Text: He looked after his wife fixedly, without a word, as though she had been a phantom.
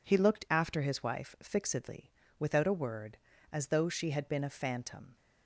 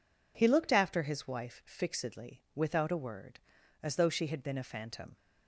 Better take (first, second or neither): neither